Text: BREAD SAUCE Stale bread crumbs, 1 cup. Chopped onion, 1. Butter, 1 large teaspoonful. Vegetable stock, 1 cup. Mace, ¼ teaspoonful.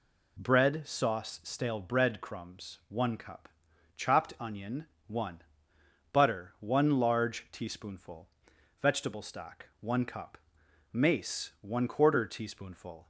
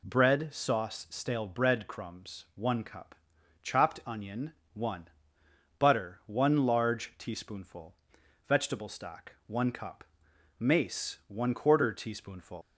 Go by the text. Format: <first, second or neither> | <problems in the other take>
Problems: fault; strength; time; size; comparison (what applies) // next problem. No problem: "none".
first | leaves "teaspoonful" unfinished; at 12.6 s; 125 ms